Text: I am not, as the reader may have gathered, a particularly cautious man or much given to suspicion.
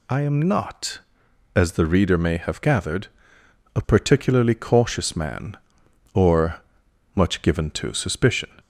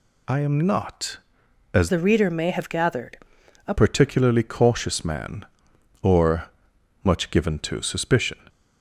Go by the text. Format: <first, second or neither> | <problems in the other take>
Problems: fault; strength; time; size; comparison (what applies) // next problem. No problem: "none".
first | changes voice from "the" to "a"; from 1.8 to 3.7 s; 1.9 s long // pauses between "or" and "much"; noticeable; at 6.5 s; 0.52 s long; noticeable in the first